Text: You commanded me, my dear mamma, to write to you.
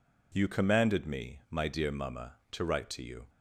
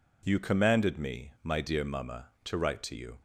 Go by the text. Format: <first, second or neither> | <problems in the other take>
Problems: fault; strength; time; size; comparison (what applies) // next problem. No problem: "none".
neither | none